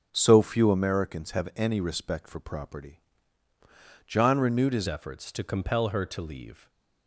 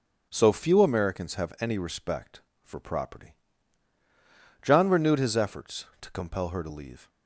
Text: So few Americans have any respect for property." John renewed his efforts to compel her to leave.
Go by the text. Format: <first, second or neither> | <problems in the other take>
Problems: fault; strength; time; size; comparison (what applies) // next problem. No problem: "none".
second | starts louder than the rest; strong; until 1.1 s; 8 dB; also in the second // changes voice at "efforts"; from 4.8 s on; 1.8 s long // stays silent after the last word; slight; from 6.5 s on; 0.5 s long